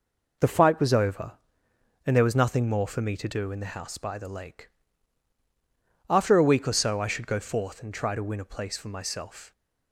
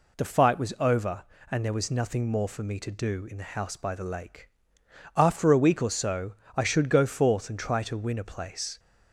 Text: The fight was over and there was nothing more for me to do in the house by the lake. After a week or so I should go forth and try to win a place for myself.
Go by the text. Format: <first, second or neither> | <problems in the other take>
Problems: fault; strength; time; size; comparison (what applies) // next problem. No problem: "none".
first | pauses between "so" and "I"; slight; at 6.3 s; 0.22 s long // stops before "for myself"; at 8.7 s